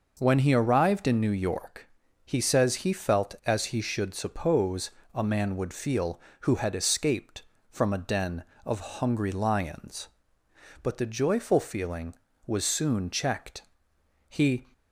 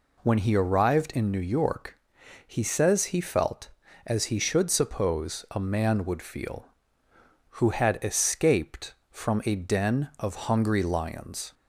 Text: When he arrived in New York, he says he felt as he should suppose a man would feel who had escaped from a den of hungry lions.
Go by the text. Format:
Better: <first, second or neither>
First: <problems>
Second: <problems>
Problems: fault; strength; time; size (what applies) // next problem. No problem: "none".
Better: second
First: pauses between "suppose" and "a"; slight; at 4.9 s; 0.24 s long // goes on to say "But the joyful feeling was soon checked He"; strong; from 10.8 s on; 3.8 s long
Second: none